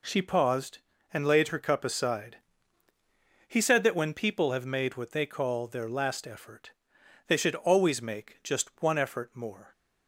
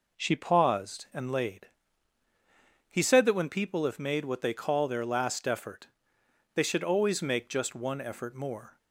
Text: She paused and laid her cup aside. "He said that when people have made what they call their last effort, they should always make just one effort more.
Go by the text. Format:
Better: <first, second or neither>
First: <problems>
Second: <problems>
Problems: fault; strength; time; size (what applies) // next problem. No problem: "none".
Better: first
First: none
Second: skips "her cup aside"; at 2.2 s